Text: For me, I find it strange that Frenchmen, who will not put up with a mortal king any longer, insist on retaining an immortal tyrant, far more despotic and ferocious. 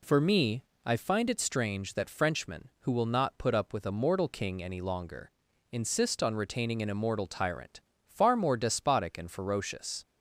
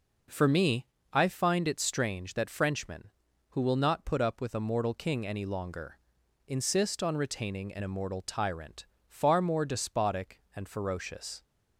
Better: neither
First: none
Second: none

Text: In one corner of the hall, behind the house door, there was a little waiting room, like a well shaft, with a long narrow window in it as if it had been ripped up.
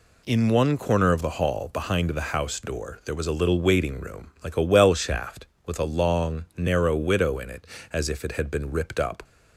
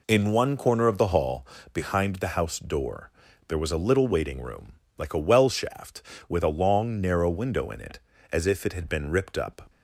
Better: second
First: says "widow" for "window"; at 6.9 s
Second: none

